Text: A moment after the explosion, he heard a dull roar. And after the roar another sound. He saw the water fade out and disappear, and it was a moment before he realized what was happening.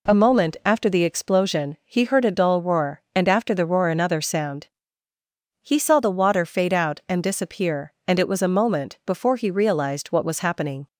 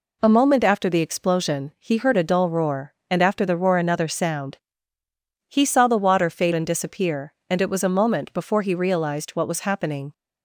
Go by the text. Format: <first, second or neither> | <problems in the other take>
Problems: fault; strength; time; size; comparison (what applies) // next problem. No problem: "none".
first | skips "out"; at 6.5 s